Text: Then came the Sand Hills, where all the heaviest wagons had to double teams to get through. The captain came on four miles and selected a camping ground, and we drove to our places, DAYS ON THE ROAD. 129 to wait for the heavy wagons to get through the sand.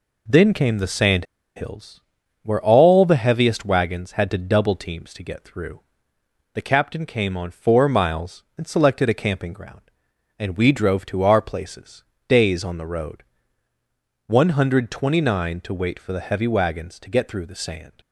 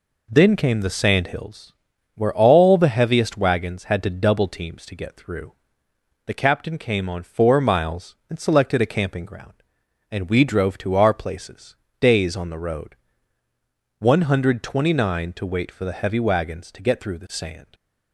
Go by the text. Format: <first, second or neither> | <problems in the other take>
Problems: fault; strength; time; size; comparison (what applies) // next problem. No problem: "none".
second | pauses between "Sand" and "Hills"; slight; at 1.2 s; 0.31 s long